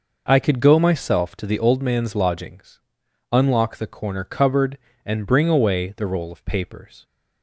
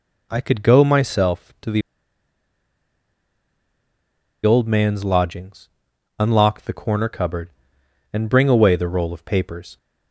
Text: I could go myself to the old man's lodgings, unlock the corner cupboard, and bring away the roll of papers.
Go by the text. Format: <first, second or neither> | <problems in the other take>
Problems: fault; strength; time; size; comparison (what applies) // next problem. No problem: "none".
first | pauses between "the" and "old"; strong; at 1.8 s; 2.6 s long